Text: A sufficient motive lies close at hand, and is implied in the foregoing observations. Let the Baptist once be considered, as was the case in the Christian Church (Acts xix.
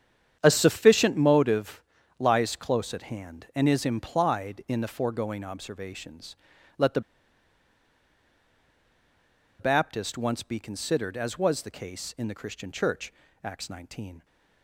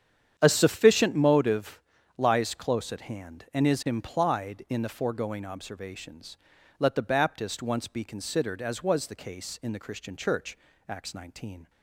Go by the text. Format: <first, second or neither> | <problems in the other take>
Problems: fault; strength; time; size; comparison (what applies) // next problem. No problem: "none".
second | starts louder than the rest; strong; until 1.4 s; 8.5 dB; strong in the second // pauses between "motive" and "lies"; slight; at 1.8 s; 0.34 s long; slight in the second // pauses between "the" and "Baptist"; strong; at 7.0 s; 2.5 s long